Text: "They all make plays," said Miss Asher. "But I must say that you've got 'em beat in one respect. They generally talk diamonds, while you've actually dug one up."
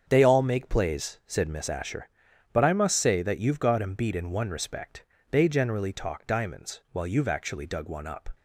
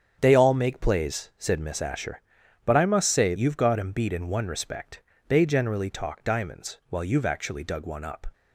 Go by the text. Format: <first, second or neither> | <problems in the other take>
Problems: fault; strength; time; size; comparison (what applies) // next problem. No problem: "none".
first | starts louder than the rest; strong; until 1.2 s; 8 dB; strong in the first // skips "that"; at 3.3 s